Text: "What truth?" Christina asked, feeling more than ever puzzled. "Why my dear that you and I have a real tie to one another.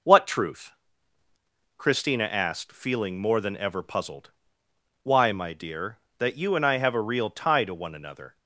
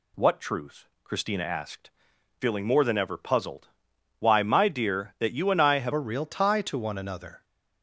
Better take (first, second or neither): first